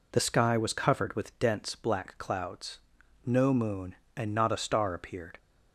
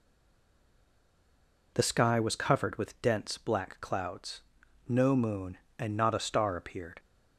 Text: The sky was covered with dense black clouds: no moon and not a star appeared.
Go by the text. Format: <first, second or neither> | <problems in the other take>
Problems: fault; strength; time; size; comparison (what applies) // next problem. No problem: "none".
first | stays silent before the first word; noticeable; until 1.7 s; 1.7 s long